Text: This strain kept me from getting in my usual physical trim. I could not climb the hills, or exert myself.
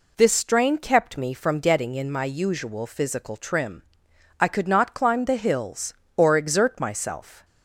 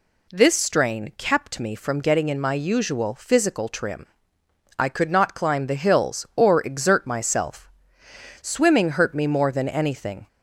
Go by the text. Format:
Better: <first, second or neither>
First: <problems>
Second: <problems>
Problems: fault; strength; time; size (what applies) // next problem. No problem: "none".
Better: first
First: none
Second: goes on to say "Swimming hurt me more than anything"; strong; from 8.4 s on; 1.8 s long